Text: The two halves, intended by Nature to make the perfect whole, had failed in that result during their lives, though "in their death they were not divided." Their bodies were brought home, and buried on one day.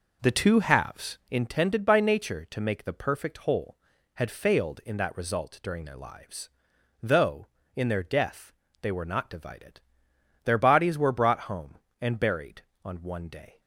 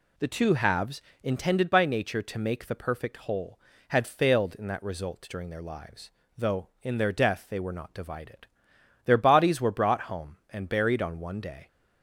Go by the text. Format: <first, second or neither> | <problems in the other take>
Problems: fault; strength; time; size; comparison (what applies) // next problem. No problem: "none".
second | starts louder than the rest; noticeable; until 1.4 s; 5 dB // pauses between "death" and "they"; slight; at 8.5 s; 0.28 s long